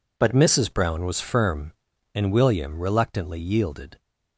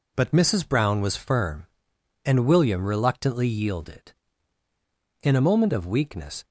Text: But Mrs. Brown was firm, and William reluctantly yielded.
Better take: first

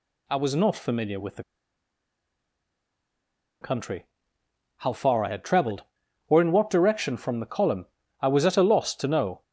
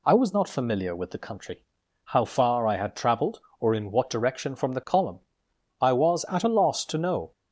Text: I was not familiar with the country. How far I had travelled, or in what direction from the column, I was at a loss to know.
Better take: second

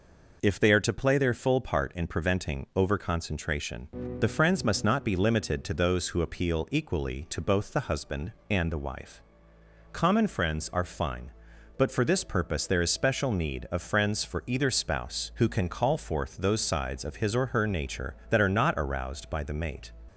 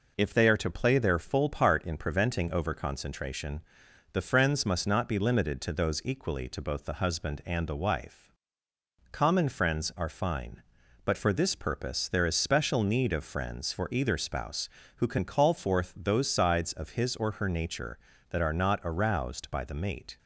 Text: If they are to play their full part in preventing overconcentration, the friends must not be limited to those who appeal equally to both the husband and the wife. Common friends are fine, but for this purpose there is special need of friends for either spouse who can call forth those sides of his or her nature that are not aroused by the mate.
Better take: first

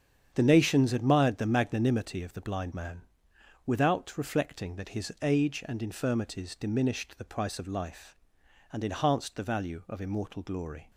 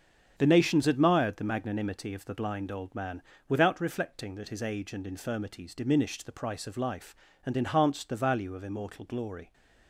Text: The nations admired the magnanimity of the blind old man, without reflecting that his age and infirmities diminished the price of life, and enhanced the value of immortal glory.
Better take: second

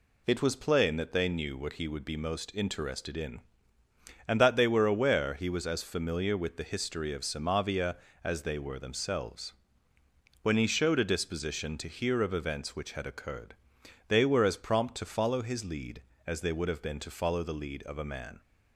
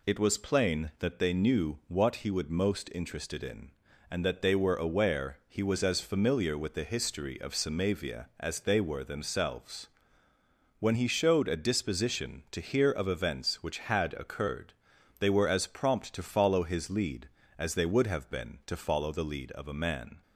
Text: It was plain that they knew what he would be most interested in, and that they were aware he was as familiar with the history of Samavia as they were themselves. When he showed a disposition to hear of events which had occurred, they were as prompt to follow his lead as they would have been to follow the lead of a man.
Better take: first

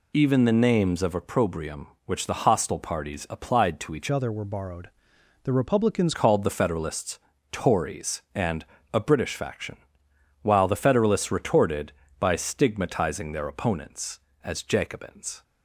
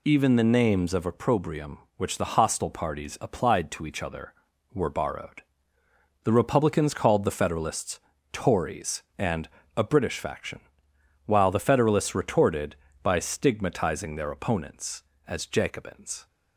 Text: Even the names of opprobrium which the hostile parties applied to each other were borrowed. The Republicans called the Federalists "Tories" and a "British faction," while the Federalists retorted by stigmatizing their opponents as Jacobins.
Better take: second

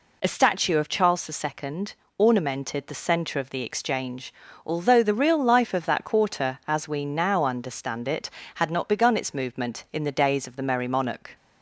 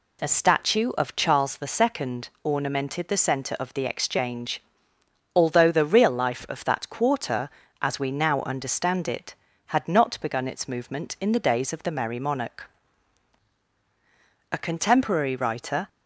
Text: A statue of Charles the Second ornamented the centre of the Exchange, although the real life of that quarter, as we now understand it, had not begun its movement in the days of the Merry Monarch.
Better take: first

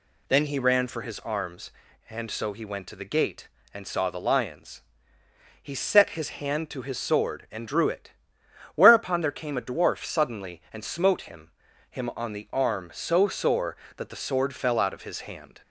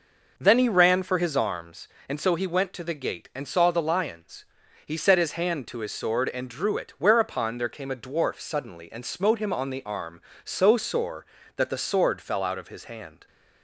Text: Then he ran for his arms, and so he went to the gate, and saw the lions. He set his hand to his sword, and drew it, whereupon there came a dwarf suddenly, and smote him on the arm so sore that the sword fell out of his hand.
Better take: second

